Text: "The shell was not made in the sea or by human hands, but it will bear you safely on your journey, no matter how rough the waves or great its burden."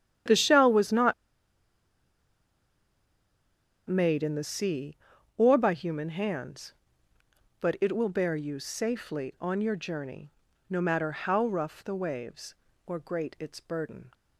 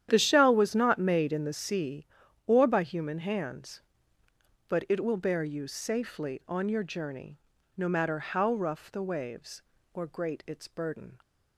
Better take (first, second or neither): second